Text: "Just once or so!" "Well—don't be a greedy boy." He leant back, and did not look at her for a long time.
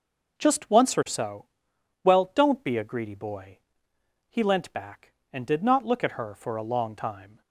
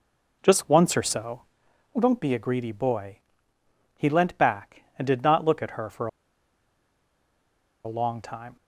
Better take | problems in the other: first | pauses between "for" and "a"; strong; at 6.0 s; 1.7 s long

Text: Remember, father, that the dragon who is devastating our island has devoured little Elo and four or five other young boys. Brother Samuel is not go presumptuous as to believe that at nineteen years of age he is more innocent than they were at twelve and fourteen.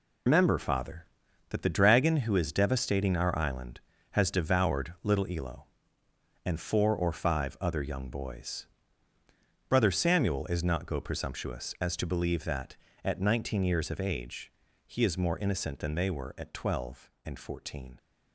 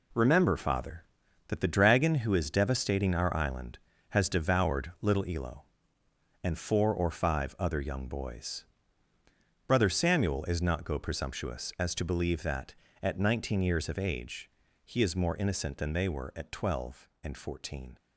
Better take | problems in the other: second | loses the start of "Remember"; at 0.2 s; 140 ms // pauses between "age" and "he"; slight; at 14.5 s; 0.34 s long; slight in the second

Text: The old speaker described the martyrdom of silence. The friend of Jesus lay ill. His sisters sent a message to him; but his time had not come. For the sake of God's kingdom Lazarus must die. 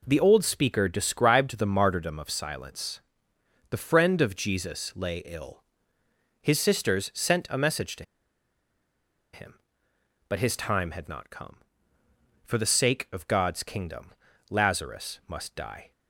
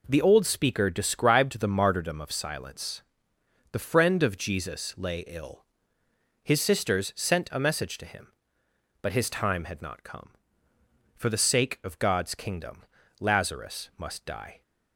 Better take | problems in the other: second | pauses between "to" and "him"; strong; at 8.0 s; 1.2 s long // pauses between "kingdom" and "Lazarus"; at 14.1 s; 0.38 s long; also in the second

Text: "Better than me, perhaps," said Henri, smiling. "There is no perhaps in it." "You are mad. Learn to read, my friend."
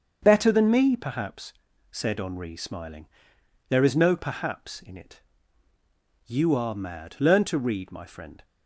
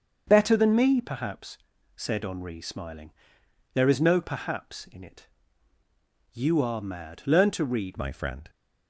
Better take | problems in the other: first | starts louder than the rest; until 1.2 s; 6.5 dB; also in the first // changes voice at "my"; from 7.9 s on; 0.5 s long

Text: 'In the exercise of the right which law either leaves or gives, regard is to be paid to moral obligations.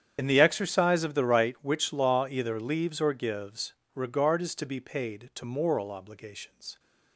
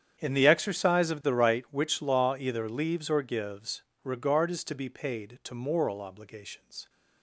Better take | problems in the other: second | loses the start of "In"; at 0.1 s; 65 ms // starts louder than the rest; strong; until 1.1 s; 9 dB; strong in the second

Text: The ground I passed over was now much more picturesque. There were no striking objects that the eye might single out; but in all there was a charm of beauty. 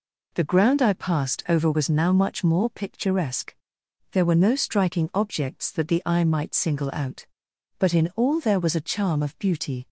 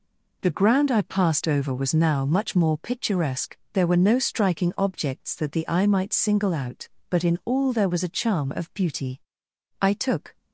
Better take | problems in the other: first | goes on to say "I took"; from 9.7 s on; 0.56 s long

